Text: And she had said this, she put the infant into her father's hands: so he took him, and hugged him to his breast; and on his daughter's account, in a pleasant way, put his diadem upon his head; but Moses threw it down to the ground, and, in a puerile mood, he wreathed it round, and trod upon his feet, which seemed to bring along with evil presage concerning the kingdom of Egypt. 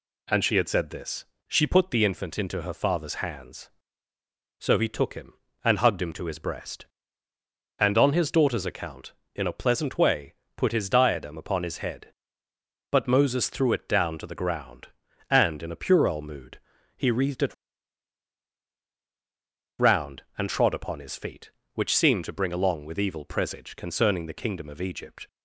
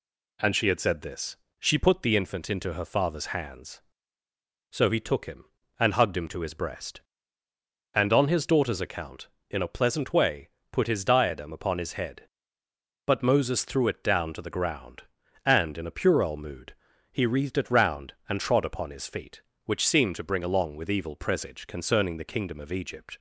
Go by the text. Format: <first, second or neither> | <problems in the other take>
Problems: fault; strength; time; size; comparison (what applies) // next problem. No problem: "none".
second | pauses between "it" and "round"; strong; at 17.5 s; 2.2 s long